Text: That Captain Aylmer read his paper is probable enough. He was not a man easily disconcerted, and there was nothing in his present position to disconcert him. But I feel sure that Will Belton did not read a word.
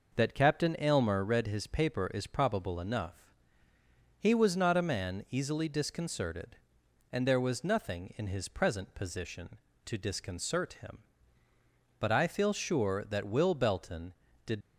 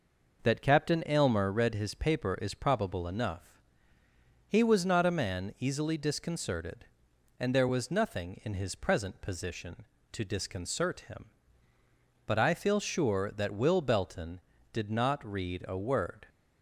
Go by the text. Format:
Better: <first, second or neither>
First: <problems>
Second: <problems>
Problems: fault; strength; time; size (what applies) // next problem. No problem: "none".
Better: second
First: stops before "not read a word"; at 14.6 s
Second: none